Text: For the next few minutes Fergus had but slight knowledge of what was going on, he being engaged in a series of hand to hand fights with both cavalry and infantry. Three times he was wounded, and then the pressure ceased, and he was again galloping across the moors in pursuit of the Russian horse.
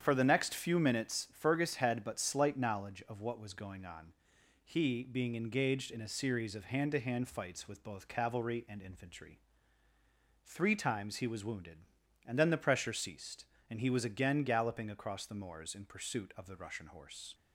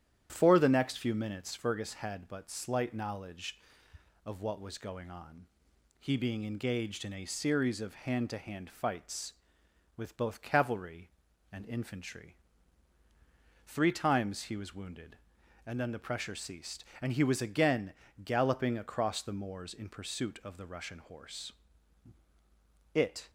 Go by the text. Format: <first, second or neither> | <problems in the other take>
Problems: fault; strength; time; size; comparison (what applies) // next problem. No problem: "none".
first | starts louder than the rest; strong; until 1.3 s; 10 dB; strong in the first // pauses between "again" and "galloping"; slight; at 17.9 s; 0.32 s long // goes on to say "It"; slight; from 22.9 s on; 0.36 s long